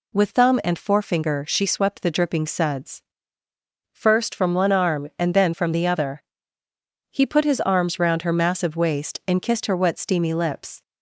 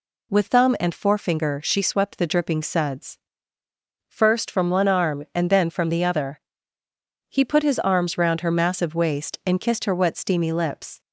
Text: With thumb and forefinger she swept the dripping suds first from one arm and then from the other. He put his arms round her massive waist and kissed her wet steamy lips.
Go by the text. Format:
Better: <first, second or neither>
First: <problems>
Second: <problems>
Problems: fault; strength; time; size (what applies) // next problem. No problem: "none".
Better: neither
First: pauses between "suds" and "first"; noticeable; at 3.0 s; 0.90 s long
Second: pauses between "suds" and "first"; noticeable; at 3.1 s; 0.90 s long